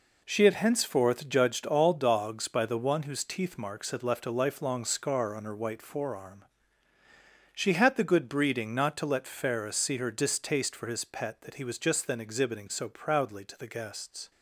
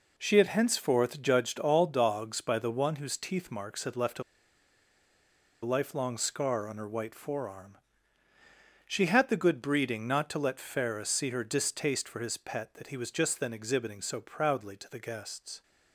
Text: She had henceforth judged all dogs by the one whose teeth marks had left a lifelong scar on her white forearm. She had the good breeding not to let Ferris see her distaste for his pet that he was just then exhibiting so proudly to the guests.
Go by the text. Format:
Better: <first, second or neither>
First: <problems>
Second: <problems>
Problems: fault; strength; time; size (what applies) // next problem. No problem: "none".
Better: first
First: none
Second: pauses between "a" and "lifelong"; strong; at 4.2 s; 1.4 s long